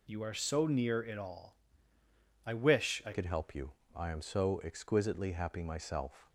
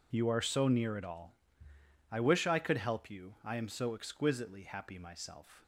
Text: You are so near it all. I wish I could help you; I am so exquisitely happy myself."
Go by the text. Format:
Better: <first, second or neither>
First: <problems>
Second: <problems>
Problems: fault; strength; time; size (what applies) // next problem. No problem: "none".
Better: second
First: changes voice at "could"; from 3.1 s on; 3.1 s long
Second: none